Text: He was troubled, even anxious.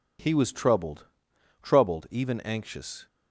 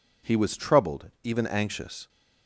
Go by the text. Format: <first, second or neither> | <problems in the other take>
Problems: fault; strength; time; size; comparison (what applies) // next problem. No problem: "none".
second | says "troubled" twice; at 1.6 s